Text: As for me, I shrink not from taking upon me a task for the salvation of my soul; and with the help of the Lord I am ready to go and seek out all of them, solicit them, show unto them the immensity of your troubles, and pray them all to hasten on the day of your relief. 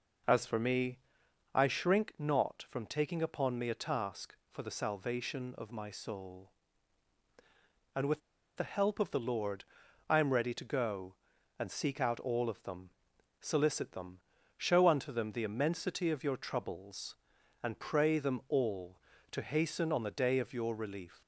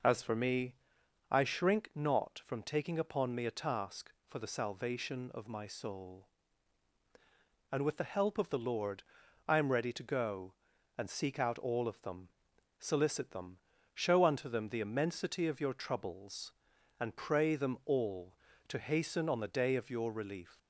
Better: second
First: pauses between "with" and "the"; at 8.2 s; 0.36 s long // pauses between "Lord" and "I"; noticeable; at 9.6 s; 0.46 s long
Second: pauses between "Lord" and "I"; noticeable; at 9.0 s; 0.46 s long

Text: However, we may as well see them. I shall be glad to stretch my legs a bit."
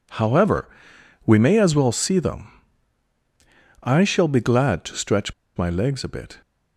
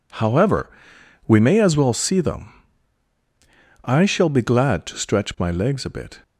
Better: second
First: pauses between "stretch" and "my"; slight; at 5.3 s; 0.25 s long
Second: none

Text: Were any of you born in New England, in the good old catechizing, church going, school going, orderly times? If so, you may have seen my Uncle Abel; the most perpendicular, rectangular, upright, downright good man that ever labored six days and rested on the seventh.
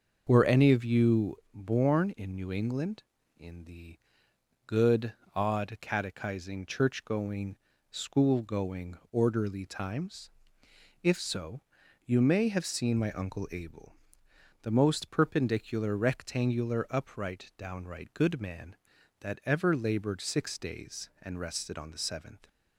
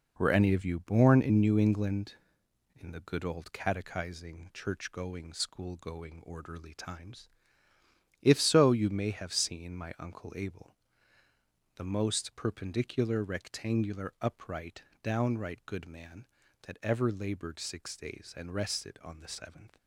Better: second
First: starts louder than the rest; noticeable; until 1.2 s; 6 dB // pauses between "you" and "born"; slight; at 1.3 s; 0.16 s long // pauses between "the" and "good"; noticeable; at 3.9 s; 0.68 s long // says "odd" for "old"; at 5.3 s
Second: none

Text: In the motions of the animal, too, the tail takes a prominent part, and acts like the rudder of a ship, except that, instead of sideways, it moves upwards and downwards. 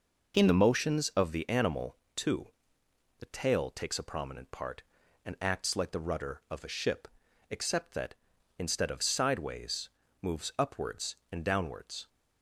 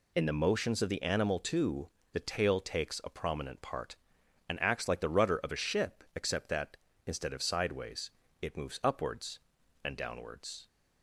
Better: second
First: skips "it"; at 10.0 s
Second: none

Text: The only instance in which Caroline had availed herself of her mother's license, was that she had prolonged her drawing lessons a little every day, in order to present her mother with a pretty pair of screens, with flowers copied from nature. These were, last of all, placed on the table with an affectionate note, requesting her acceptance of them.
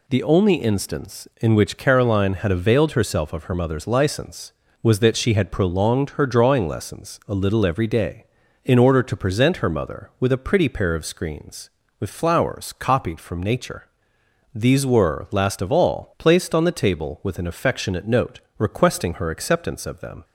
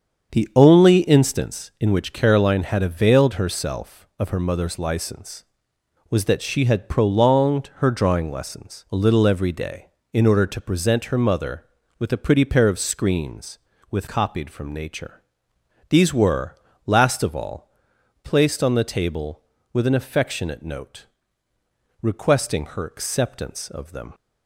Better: first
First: none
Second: starts louder than the rest; until 1.4 s; 7 dB // skips "flowers"; at 14.0 s

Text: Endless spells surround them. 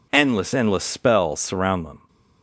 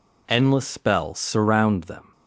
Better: second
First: says "Endless" twice; at 0.5 s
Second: none

